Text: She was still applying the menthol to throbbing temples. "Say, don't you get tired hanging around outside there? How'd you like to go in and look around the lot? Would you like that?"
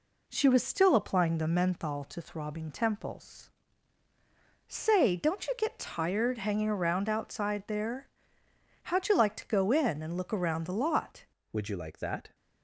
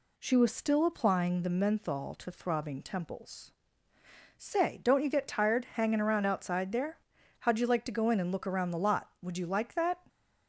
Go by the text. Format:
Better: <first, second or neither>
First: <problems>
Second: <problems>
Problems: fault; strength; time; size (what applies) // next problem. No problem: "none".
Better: second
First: changes voice at "Would"; from 11.5 s on; 0.8 s long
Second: none